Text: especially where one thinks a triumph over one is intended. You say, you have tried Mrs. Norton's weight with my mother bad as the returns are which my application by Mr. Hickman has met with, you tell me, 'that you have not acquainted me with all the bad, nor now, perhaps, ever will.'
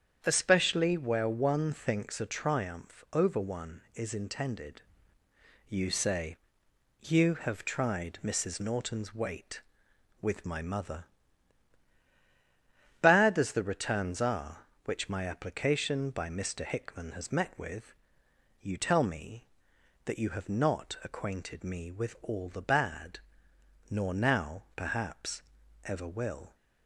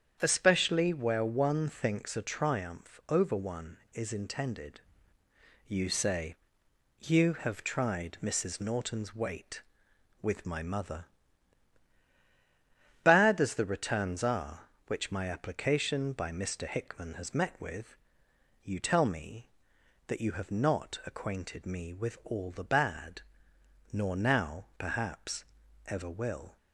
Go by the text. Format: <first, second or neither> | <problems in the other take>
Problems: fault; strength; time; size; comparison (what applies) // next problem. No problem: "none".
neither | starts louder than the rest; strong; the same in both // pauses between "mother" and "bad"; strong; the same in both